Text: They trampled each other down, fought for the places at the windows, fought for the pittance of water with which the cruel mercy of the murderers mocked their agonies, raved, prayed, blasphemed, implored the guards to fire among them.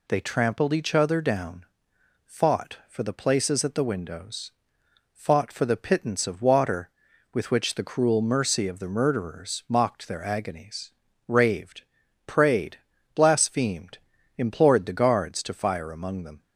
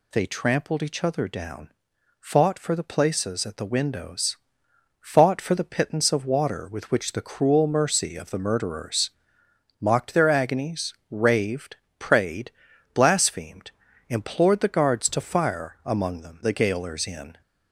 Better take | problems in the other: first | pauses between "murderers" and "mocked"; noticeable; at 9.1 s; 0.72 s long // goes on to say "The gaolers in"; noticeable; from 16.4 s on; 0.98 s long

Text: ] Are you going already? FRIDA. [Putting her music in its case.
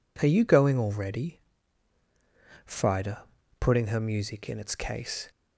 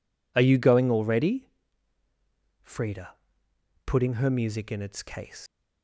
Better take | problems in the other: first | leaves "case" unfinished; at 5.4 s; 135 ms

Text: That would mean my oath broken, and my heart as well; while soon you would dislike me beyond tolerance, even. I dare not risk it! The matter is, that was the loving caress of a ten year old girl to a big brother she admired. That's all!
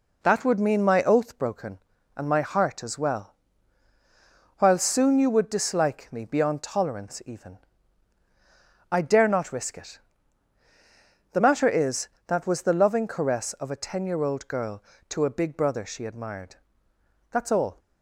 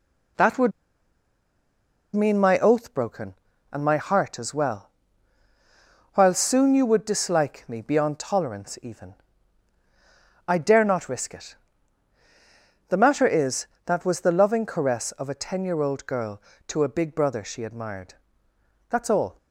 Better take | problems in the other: first | pauses between "would" and "mean"; strong; at 0.7 s; 1.4 s long

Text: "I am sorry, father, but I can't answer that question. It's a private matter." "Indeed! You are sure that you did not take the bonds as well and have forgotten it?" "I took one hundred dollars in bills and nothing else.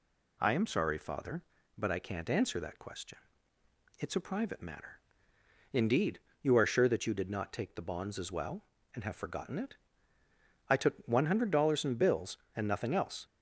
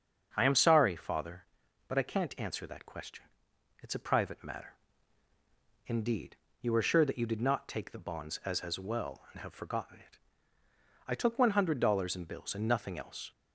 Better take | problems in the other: first | starts louder than the rest; strong; until 1.3 s; 7.5 dB // says "as" twice; at 8.6 s

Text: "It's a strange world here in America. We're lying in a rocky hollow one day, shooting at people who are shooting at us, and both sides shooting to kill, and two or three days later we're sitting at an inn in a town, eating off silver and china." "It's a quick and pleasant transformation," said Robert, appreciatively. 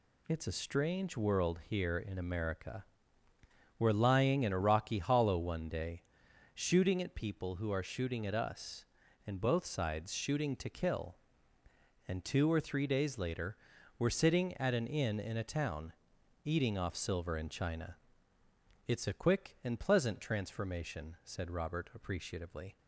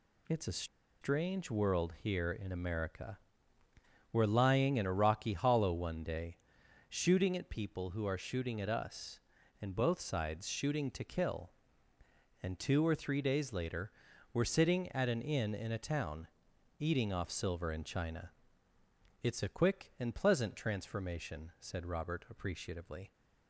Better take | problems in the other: first | pauses between "a" and "strange"; slight; at 0.6 s; 0.36 s long // pauses between "later" and "we're"; at 13.9 s; 0.40 s long; also in the first

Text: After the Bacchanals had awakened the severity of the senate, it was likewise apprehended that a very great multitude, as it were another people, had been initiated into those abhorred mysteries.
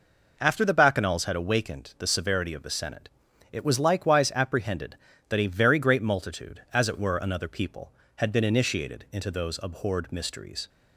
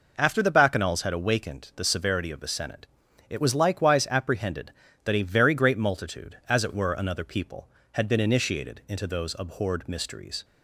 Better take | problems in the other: neither | none

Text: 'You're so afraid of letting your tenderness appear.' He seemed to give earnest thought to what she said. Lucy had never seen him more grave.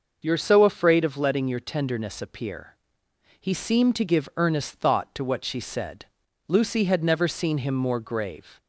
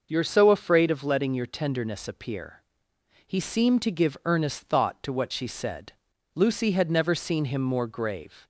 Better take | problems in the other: neither | starts louder than the rest; noticeable; the same in both

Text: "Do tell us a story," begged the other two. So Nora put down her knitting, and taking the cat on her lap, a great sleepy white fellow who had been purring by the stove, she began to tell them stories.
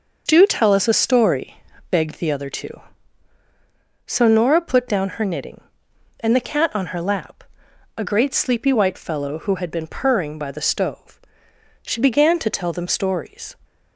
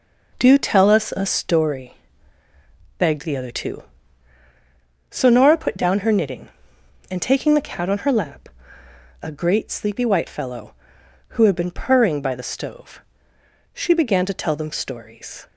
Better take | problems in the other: second | skips "taking"; at 6.3 s

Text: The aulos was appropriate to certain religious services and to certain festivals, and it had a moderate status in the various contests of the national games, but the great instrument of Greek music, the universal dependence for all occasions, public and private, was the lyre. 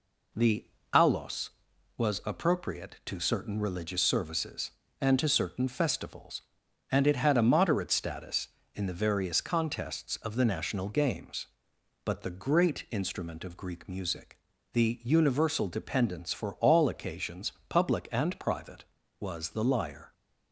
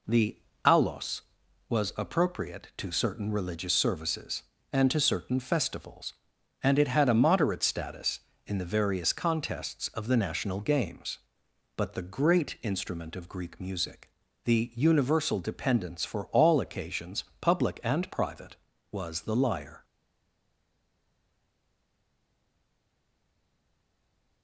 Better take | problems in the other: first | pauses between "The" and "aulos"; slight; at 0.3 s; 0.26 s long; slight in the first // stays silent after the last word; strong; from 19.8 s on; 4.6 s long

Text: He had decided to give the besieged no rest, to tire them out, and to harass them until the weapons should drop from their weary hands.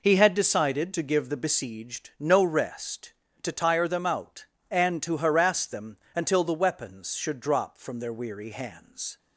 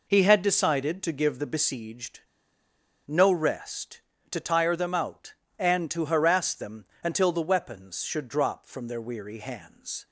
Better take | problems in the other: first | pauses between "besieged" and "no"; noticeable; at 2.1 s; 0.86 s long // pauses between "them" and "until"; slight; at 6.8 s; 0.18 s long; slight in the first

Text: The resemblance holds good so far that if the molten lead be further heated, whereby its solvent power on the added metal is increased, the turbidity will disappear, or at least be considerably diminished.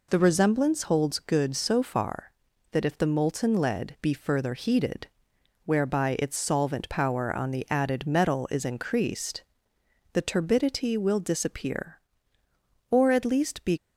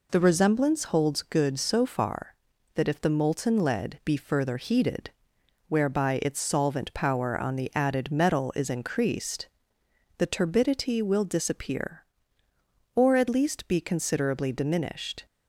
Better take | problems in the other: second | stops before "considerably diminished"; at 13.7 s

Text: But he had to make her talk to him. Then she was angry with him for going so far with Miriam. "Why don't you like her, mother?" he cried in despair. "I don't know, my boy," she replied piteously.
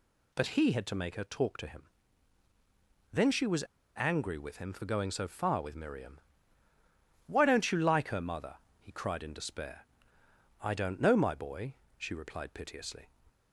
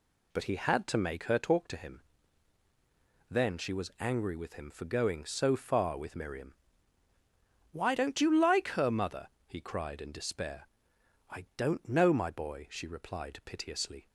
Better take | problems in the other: second | pauses between "was" and "angry"; slight; at 3.6 s; 0.32 s long

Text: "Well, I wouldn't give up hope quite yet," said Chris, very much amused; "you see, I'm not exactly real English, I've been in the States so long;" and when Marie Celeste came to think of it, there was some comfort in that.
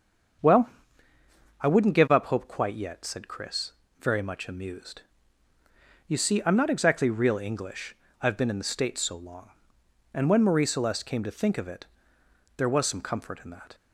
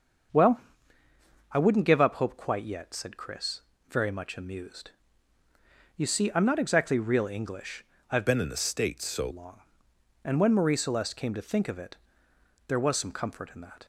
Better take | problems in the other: first | starts louder than the rest; until 2.2 s; 6.5 dB; also in the first // changes voice from "been" to "so"; from 8.2 to 9.2 s; 1.0 s long

